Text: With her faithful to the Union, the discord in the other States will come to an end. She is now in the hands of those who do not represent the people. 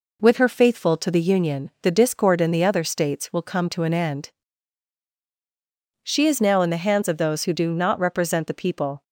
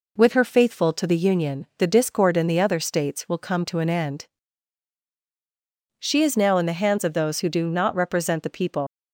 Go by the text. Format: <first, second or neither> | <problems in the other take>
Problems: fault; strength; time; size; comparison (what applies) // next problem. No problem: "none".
first | leaves "people" unfinished; at 8.8 s; 120 ms